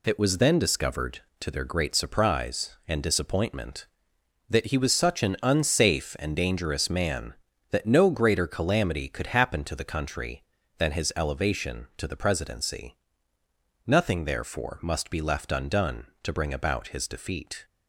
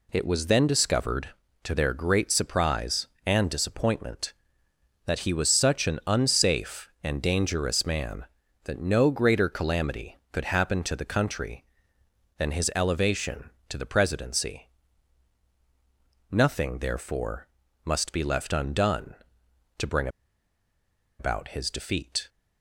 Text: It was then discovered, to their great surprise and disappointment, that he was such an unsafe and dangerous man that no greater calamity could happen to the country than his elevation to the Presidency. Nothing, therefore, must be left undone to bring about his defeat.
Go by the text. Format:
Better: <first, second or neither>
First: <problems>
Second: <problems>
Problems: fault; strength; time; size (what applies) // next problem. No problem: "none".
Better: first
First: none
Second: pauses between "bring" and "about"; at 20.0 s; 1.1 s long